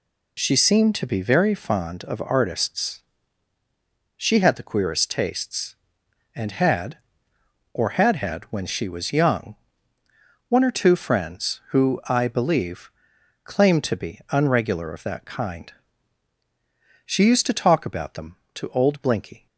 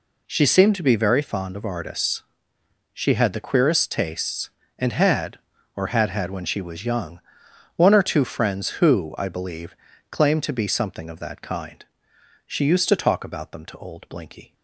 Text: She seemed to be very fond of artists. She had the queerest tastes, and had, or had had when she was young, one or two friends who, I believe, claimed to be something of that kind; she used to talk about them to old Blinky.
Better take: second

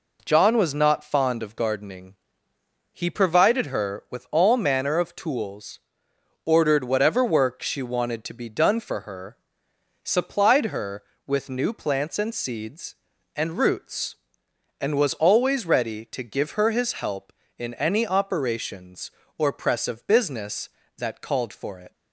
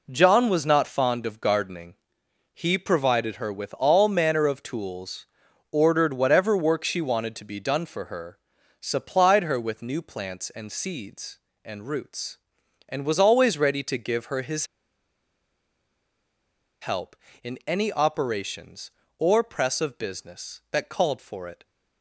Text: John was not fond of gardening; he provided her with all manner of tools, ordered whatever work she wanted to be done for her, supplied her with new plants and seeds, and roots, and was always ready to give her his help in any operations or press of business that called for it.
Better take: first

